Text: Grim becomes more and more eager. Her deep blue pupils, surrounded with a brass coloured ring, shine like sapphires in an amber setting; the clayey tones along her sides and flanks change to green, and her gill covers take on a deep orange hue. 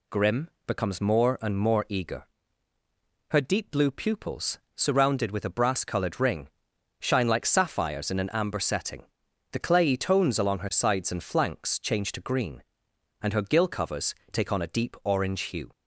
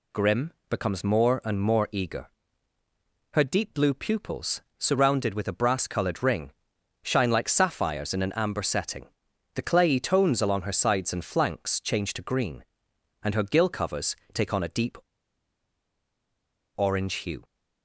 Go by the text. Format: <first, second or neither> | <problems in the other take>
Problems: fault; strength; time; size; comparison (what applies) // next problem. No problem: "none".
first | pauses between "Grim" and "becomes"; slight; at 0.5 s; 0.18 s long; slight in the first // pauses between "covers" and "take"; slight; at 14.1 s; 0.16 s long; slight in the first // pauses between "deep" and "orange"; strong; at 14.9 s; 1.7 s long